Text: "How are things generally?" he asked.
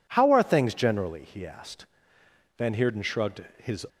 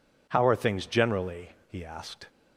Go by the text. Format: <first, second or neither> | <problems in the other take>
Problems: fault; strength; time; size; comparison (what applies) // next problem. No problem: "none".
second | goes on to say "Van Heerden shrugged his"; noticeable; from 2.5 s on; 1.3 s long